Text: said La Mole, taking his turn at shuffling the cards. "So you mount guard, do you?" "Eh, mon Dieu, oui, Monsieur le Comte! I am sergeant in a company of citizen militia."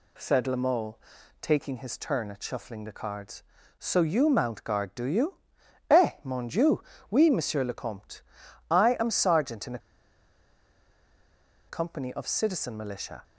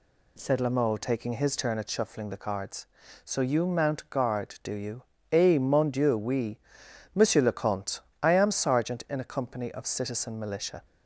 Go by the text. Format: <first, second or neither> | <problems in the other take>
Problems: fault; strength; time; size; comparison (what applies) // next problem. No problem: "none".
second | pauses between "a" and "company"; strong; at 9.7 s; 1.9 s long